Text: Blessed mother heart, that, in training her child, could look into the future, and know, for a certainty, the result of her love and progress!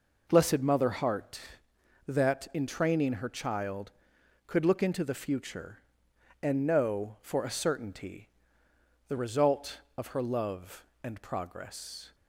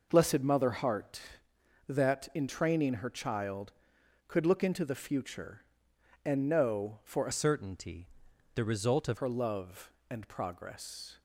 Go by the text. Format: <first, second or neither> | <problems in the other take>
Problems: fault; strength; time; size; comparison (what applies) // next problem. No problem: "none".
first | changes voice from "certainty" to "of"; from 7.3 to 9.1 s; 1.8 s long